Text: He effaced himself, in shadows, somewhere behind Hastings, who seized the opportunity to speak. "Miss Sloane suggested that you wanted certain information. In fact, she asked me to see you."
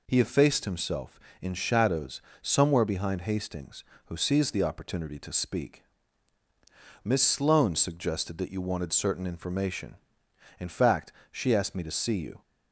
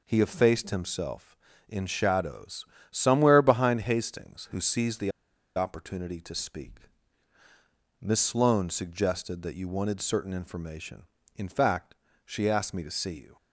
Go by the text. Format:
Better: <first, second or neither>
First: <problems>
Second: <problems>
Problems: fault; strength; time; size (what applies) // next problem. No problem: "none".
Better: first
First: none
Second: pauses between "the" and "opportunity"; at 5.1 s; 0.44 s long